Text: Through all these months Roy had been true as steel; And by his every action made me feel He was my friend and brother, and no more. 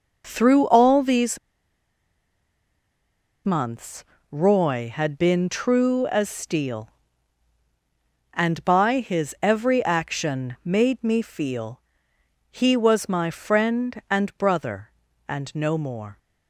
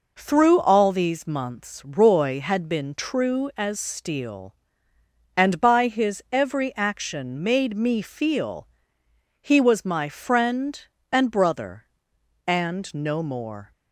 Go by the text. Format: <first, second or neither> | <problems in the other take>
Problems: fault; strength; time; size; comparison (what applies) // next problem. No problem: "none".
second | pauses between "these" and "months"; strong; at 1.3 s; 2.0 s long // pauses between "months" and "Roy"; slight; at 4.0 s; 0.28 s long // pauses between "feel" and "He"; noticeable; at 11.8 s; 0.68 s long; noticeable in the second